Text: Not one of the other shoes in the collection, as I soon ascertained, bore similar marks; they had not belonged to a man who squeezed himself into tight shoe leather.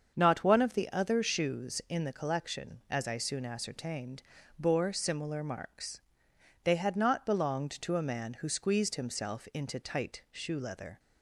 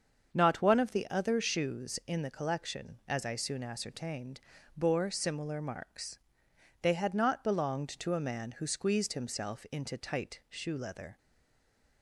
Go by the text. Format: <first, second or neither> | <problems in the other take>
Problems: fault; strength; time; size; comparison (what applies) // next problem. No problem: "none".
first | starts louder than the rest; until 1.3 s; 7 dB; also in the first // stays silent after the last word; slight; from 11.1 s on; 0.9 s long